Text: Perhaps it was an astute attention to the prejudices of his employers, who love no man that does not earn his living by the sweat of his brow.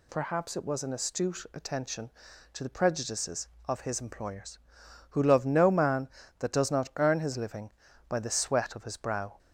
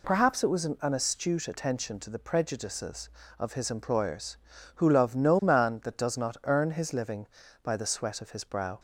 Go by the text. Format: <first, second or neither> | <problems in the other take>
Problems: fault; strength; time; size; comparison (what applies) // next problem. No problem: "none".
first | says "an" twice; at 0.8 s